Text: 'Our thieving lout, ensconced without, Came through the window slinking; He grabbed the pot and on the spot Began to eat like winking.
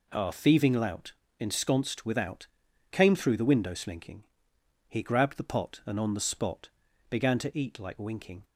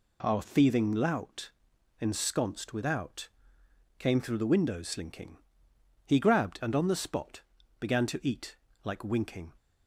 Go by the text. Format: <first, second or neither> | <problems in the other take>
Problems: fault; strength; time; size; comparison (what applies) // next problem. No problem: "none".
first | skips "the pot"; at 6.6 s // pauses between "spot" and "Began"; at 7.4 s; 0.38 s long; also in the first // pauses between "eat" and "like"; slight; at 8.5 s; 0.28 s long